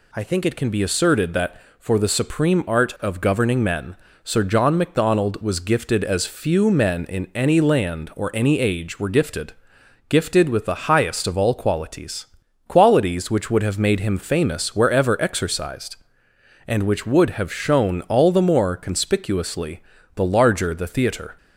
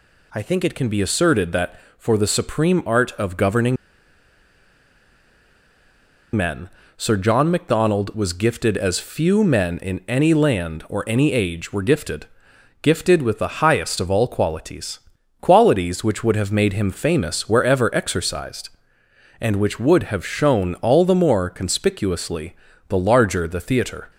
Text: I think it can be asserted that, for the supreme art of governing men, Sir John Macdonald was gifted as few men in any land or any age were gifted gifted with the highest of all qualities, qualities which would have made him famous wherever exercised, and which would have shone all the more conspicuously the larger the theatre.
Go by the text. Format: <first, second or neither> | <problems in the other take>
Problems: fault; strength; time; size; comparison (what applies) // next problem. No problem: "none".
first | pauses between "governing" and "men"; strong; at 3.7 s; 2.6 s long // pauses between "gifted" and "gifted"; noticeable; at 12.2 s; 0.56 s long; noticeable in the first // pauses between "conspicuously" and "the"; slight; at 22.5 s; 0.34 s long; slight in the first